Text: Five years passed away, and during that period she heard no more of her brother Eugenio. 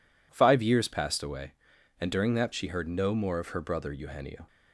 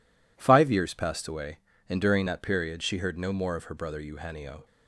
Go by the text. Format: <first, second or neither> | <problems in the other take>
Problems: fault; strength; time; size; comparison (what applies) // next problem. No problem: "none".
second | skips "period"; at 2.5 s